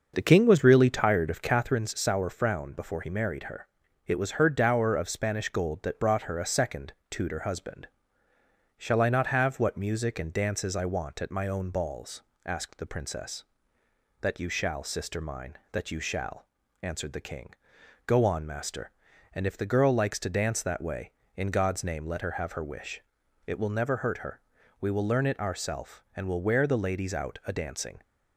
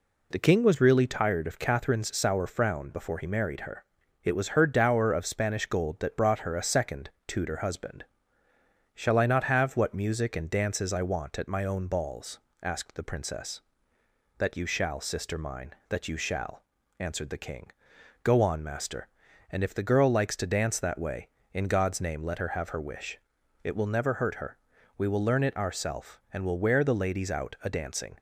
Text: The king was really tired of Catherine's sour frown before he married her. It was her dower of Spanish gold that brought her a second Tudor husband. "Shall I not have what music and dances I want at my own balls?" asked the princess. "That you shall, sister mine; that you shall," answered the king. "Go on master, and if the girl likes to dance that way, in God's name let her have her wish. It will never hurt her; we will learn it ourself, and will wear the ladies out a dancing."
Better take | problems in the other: second | starts louder than the rest; until 1.8 s; 6 dB // pauses between "second" and "Tudor"; slight; at 6.9 s; 0.18 s long; slight in the second

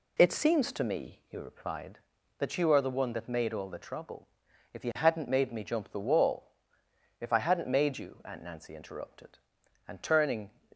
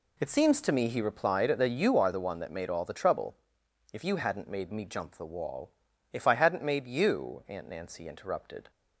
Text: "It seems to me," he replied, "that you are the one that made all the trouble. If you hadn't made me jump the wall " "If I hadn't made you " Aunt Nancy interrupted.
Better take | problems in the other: second | goes on to say "And turning"; noticeable; from 9.8 s on; 0.64 s long

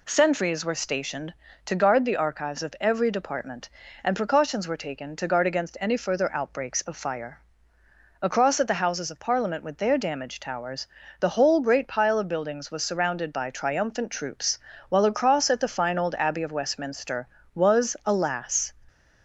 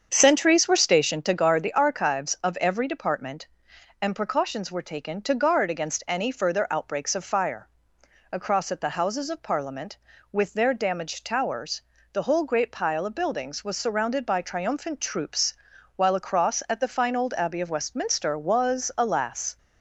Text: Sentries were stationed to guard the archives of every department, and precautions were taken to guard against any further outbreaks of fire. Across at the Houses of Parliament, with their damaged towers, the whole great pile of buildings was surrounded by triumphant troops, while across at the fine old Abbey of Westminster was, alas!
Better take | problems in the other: first | starts louder than the rest; strong; until 1.4 s; 7.5 dB

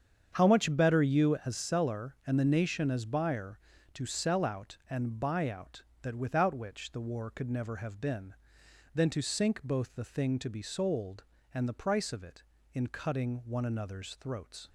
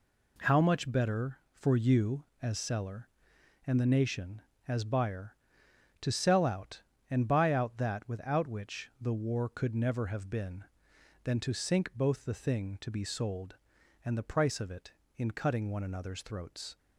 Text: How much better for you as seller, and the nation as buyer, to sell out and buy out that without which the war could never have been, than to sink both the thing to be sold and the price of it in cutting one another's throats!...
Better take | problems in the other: second | starts louder than the rest; strong; until 1.3 s; 7.5 dB // skips "for"; at 1.0 s

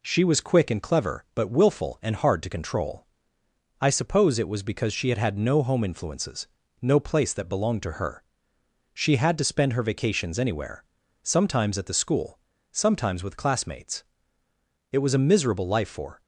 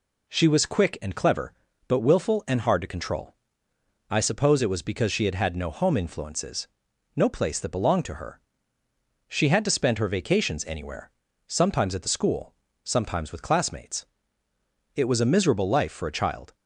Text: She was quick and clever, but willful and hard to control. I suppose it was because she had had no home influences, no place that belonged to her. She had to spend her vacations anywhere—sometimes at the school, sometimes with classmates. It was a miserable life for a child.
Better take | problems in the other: second | stops before "a child"; at 16.2 s

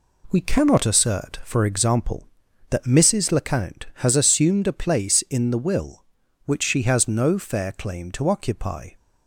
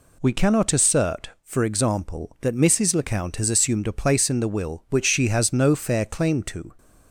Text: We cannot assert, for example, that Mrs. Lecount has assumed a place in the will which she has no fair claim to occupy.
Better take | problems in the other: first | stops before "occupy"; at 6.7 s

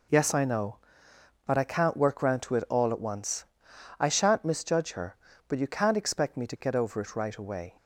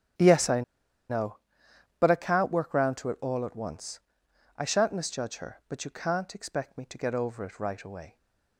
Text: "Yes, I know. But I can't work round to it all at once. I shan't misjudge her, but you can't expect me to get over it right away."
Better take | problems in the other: first | starts louder than the rest; strong; until 2.2 s; 10.5 dB // pauses between "I" and "know"; noticeable; at 0.6 s; 0.47 s long

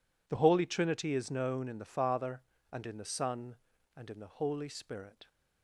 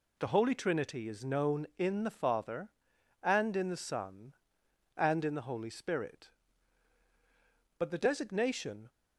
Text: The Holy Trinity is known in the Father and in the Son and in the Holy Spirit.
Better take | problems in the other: first | goes on to say "But the designation"; noticeable; from 7.7 s on; 1.1 s long

